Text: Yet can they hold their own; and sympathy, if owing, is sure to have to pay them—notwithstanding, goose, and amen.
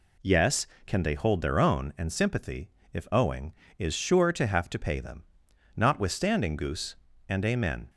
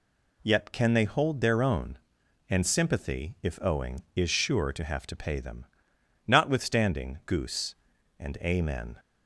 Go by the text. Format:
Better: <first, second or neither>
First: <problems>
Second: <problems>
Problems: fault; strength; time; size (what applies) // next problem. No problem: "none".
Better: second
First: says "Yes" for "Yet"; at 0.2 s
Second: none